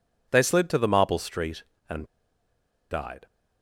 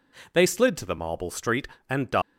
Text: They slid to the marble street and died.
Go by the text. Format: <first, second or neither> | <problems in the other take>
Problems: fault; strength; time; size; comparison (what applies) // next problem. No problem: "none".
second | pauses between "and" and "died"; noticeable; at 2.0 s; 0.87 s long